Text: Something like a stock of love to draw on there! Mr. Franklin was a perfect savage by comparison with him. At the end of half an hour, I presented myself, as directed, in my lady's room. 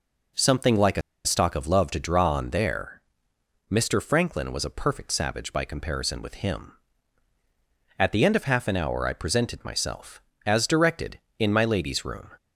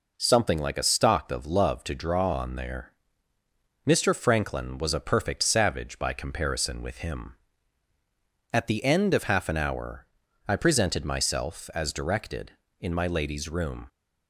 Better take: second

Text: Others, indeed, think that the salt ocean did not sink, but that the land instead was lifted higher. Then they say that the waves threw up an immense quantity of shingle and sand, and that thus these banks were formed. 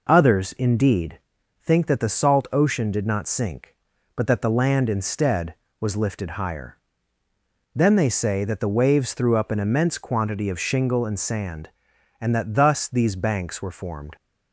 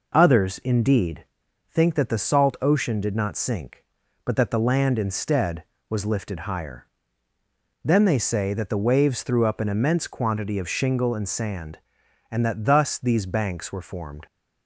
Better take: neither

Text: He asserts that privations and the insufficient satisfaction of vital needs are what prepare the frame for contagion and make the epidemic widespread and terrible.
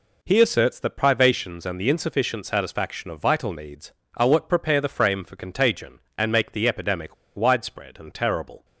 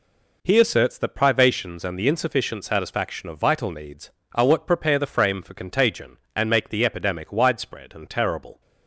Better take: second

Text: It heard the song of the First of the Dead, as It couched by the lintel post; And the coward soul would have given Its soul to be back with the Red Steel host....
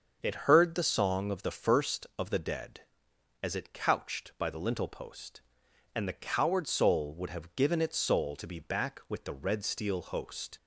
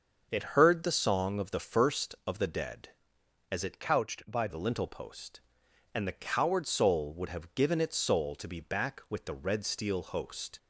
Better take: first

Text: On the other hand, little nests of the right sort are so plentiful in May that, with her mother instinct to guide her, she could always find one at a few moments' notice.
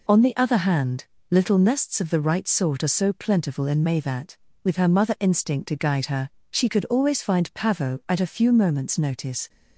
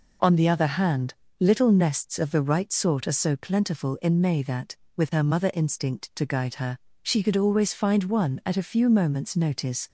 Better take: second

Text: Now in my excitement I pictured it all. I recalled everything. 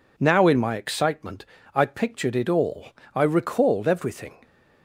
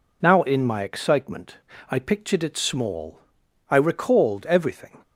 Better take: first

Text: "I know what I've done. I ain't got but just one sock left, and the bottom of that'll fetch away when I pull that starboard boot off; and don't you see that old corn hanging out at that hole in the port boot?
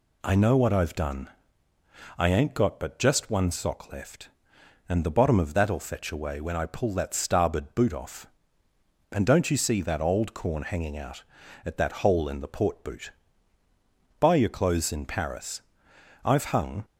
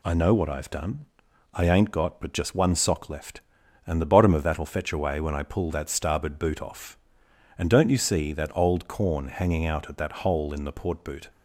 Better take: second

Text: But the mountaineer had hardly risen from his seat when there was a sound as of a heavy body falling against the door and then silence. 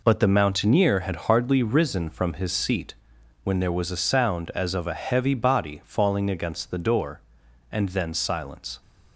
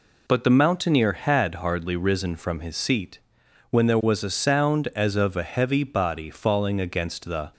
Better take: first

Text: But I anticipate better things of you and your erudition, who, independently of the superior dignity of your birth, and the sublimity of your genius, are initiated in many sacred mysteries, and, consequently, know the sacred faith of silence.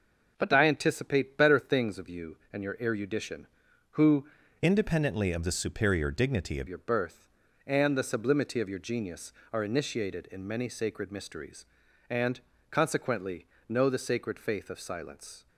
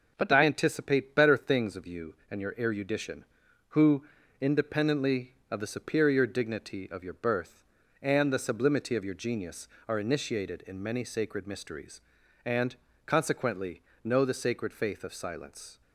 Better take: second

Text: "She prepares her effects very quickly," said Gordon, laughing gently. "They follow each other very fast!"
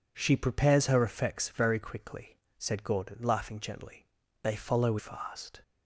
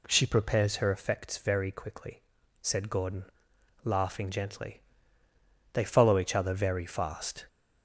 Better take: second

